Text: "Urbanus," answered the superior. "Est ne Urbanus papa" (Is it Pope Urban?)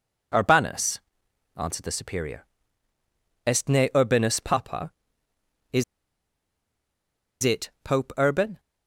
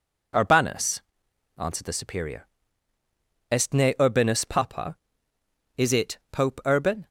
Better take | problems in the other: second | pauses between "Is" and "it"; strong; at 5.8 s; 1.5 s long

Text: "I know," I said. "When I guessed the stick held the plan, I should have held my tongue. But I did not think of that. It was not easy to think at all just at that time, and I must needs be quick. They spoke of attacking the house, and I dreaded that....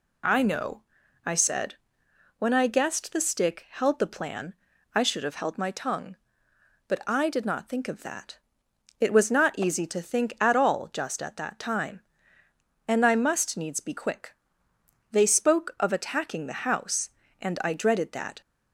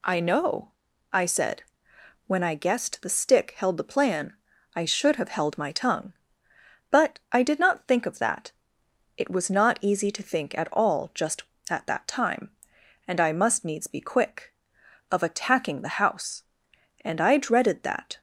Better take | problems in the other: first | skips "They spoke"; at 14.8 s

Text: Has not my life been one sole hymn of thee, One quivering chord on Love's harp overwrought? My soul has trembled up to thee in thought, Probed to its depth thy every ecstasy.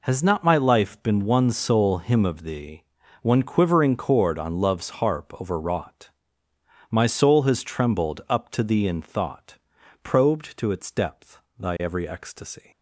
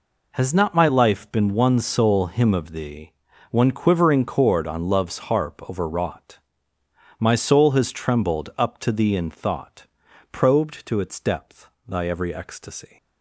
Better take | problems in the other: neither | pauses between "depth" and "thy"; slight; the same in both

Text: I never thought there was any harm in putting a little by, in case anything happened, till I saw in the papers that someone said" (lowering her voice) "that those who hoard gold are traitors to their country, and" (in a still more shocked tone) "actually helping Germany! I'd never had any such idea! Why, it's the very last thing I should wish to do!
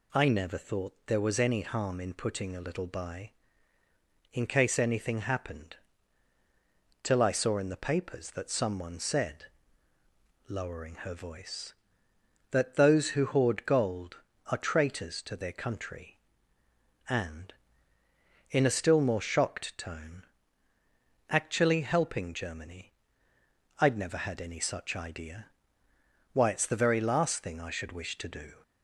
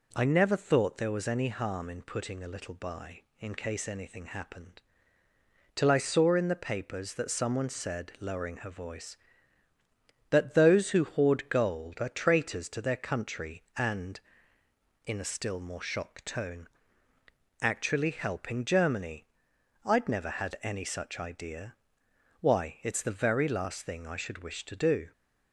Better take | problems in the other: neither | none

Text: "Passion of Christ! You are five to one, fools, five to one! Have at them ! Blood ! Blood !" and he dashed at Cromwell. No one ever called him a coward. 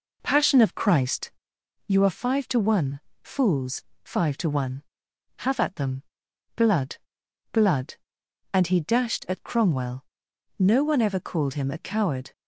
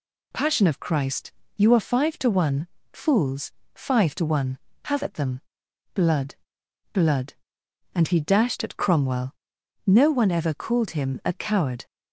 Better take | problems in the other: second | starts louder than the rest; noticeable; until 1.5 s; 4 dB

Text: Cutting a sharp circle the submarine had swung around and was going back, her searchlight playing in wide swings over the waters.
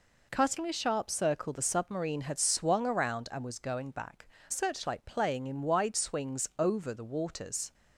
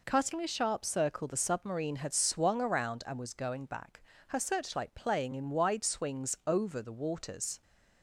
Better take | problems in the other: second | skips "her"; at 4.3 s

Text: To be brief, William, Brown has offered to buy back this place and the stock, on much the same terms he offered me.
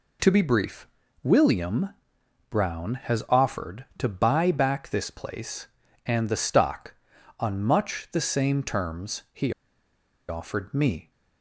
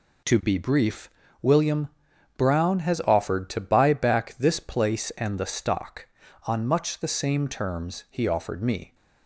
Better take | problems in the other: second | pauses between "he" and "offered"; noticeable; at 9.5 s; 0.77 s long

